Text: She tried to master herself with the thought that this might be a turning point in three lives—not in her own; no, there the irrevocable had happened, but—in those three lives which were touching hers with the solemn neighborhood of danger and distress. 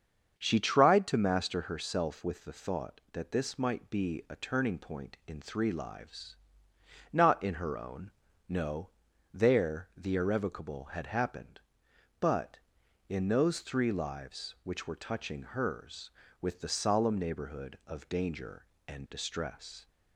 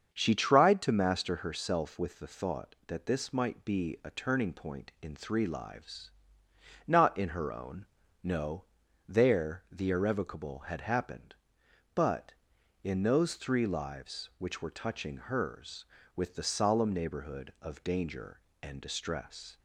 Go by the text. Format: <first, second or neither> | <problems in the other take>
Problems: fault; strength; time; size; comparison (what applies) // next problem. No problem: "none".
neither | starts louder than the rest; the same in both